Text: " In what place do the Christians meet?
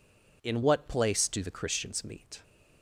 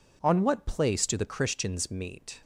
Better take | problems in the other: first | says "On" for "In"; at 0.2 s

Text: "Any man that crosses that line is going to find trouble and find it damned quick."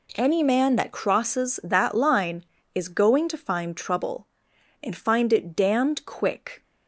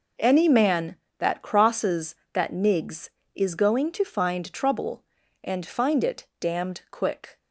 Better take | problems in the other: first | says "nigs" for "line"; at 2.5 s

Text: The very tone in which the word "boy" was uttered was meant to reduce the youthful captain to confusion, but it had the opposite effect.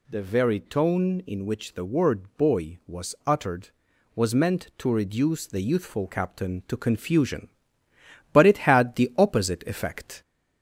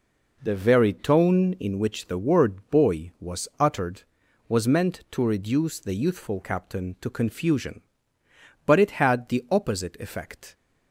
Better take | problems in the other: second | gets louder; slight; throughout; 2 dB

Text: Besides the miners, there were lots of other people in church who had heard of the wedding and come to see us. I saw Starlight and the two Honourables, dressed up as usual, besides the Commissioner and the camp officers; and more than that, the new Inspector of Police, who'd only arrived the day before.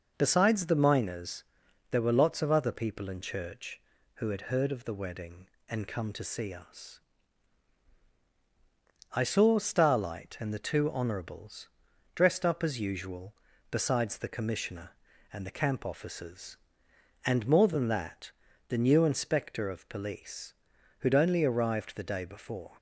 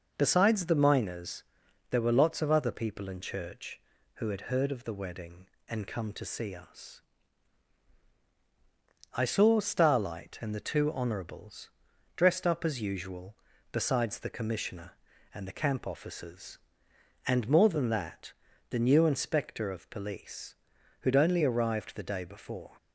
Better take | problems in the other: neither | none

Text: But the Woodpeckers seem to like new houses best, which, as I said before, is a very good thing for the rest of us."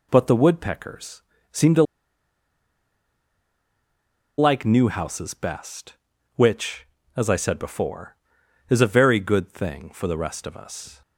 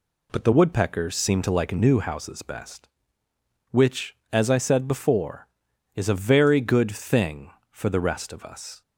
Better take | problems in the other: second | pauses between "Woodpeckers" and "seem"; slight; at 1.2 s; 0.30 s long // pauses between "to" and "like"; strong; at 1.8 s; 2.5 s long

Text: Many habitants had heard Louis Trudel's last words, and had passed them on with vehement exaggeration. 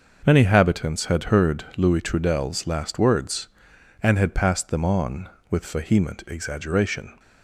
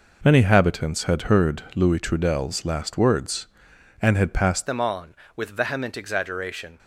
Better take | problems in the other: first | changes voice at "them"; from 4.6 s on; 2.1 s long

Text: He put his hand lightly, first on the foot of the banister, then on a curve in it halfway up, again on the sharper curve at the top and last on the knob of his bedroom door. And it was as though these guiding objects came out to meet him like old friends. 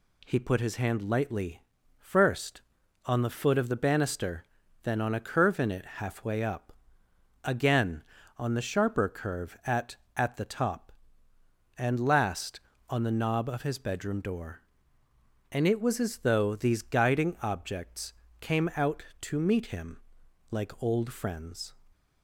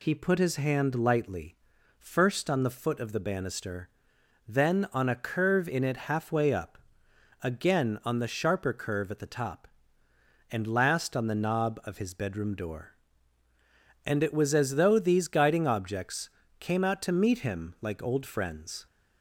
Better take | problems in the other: second | says "at" twice; at 10.1 s // pauses between "objects" and "came"; slight; at 18.1 s; 0.26 s long; slight in the second // pauses between "him" and "like"; noticeable; at 19.9 s; 0.50 s long

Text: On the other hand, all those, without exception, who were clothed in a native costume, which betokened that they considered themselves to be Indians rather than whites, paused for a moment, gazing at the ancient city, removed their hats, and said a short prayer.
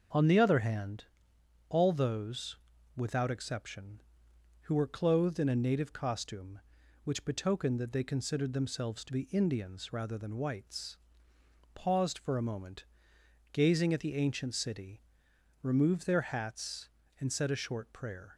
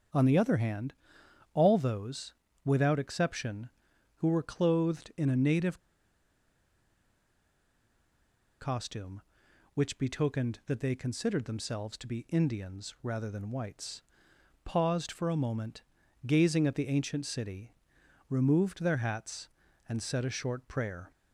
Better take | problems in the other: first | starts louder than the rest; strong; until 1.7 s; 7.5 dB; also in the first // pauses between "native" and "costume"; strong; at 5.7 s; 2.8 s long

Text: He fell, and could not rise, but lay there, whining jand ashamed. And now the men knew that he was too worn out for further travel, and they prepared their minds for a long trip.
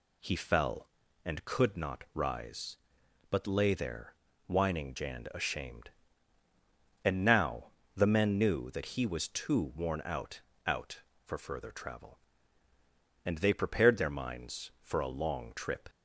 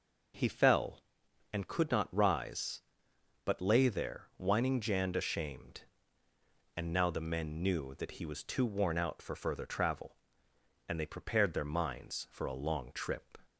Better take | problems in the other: second | pauses between "now" and "the"; slight; at 7.7 s; 0.24 s long // says "out" twice; at 10.6 s

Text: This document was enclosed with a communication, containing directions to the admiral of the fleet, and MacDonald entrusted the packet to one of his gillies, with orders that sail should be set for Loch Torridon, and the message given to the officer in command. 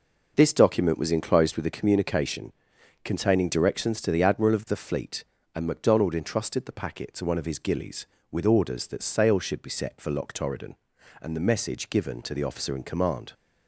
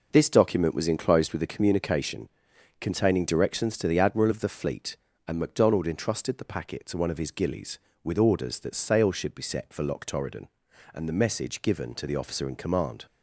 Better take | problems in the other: neither | none

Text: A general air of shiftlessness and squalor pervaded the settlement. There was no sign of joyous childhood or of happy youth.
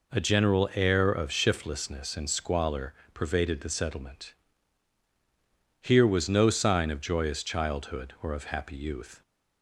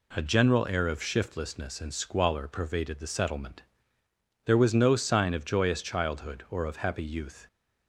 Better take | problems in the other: second | pauses between "squalor" and "pervaded"; slight; at 2.9 s; 0.20 s long // says "Here" for "There"; at 5.7 s

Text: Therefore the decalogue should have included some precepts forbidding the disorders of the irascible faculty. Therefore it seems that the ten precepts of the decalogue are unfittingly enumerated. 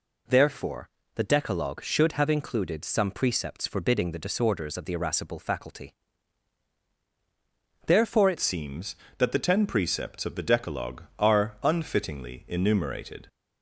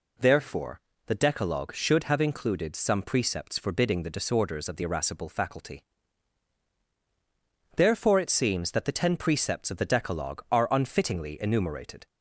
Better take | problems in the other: second | pauses between "Therefore" and "the"; slight; at 0.8 s; 0.26 s long; slight in the second // changes voice at "seems"; from 8.3 s on; 4.9 s long

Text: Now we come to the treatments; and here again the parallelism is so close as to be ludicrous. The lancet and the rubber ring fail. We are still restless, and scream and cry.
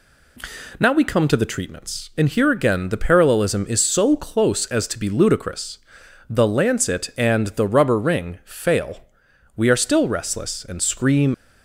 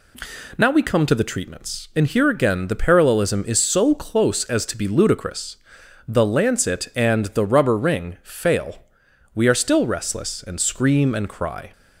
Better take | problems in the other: second | stops before "and cry"; at 11.3 s

